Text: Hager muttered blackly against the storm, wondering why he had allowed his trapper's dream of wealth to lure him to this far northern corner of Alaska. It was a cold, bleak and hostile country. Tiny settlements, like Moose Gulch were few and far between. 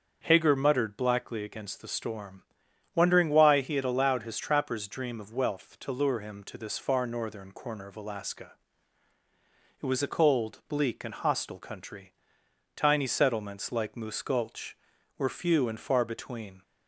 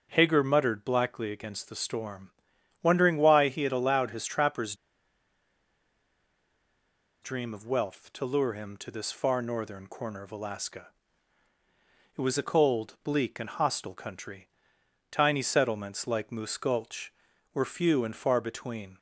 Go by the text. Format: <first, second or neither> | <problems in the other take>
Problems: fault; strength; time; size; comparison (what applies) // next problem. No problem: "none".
first | starts louder than the rest; until 1.1 s; 6.5 dB; also in the first // pauses between "trapper's" and "dream"; strong; at 4.7 s; 2.4 s long